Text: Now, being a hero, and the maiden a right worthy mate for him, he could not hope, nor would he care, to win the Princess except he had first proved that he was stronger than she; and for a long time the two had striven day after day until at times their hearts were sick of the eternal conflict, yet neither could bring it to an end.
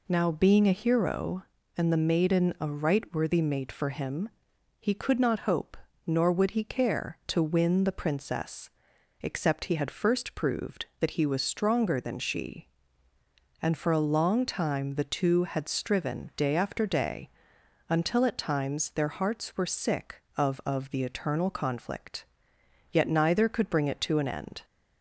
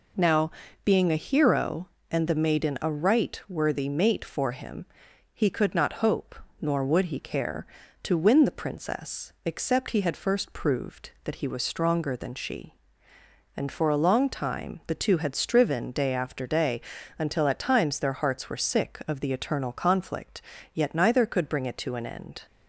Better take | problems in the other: second | pauses between "Princess" and "except"; noticeable; at 8.6 s; 0.52 s long // pauses between "day" and "until"; noticeable; at 17.2 s; 0.58 s long; also in the second // says "of" twice; at 20.6 s

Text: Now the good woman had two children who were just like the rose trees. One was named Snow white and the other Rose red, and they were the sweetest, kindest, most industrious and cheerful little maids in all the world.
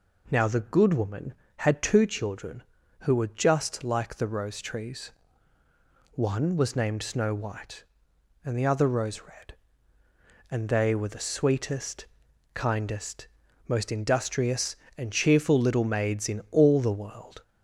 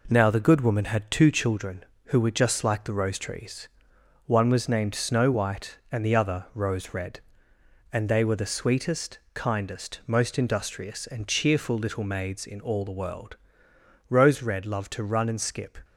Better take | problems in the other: first | goes on to say "Rose red loved to run and skip"; strong; from 14.0 s on; 1.7 s long

